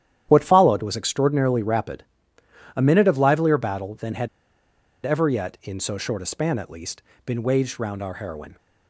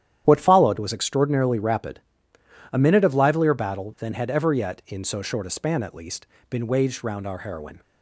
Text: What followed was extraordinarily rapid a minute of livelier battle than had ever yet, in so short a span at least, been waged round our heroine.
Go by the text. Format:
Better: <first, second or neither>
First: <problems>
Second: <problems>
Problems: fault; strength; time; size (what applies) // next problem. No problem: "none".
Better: second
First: starts louder than the rest; strong; until 1.3 s; 10.5 dB // pauses between "rapid" and "a"; noticeable; at 2.0 s; 0.72 s long // pauses between "had" and "ever"; noticeable; at 4.2 s; 0.75 s long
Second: starts louder than the rest; strong; until 1.2 s; 10.5 dB // pauses between "rapid" and "a"; noticeable; at 1.9 s; 0.72 s long